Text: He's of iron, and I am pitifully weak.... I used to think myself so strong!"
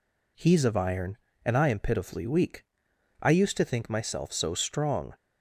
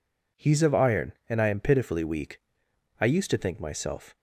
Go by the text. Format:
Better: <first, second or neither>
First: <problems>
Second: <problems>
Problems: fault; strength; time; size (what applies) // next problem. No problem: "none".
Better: first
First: none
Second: stops before "so strong"; at 4.1 s